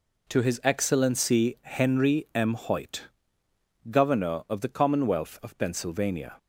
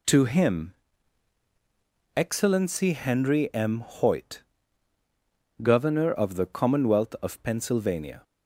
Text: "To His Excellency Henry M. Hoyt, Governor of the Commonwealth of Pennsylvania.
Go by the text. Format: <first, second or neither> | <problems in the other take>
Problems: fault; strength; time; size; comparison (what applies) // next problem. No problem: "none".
first | says "Him" for "His"; at 0.2 s